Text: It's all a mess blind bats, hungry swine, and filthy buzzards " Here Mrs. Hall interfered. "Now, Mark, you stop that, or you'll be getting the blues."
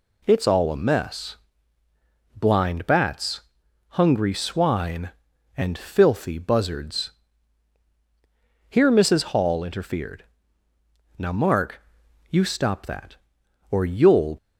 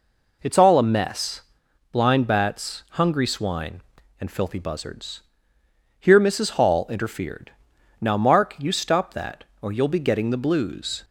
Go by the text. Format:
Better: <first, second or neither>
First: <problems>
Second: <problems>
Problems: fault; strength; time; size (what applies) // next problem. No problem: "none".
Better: second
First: pauses between "mess" and "blind"; at 1.3 s; 1.0 s long // stops before "be getting the blues"; at 14.3 s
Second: pauses between "mess" and "blind"; noticeable; at 1.4 s; 0.50 s long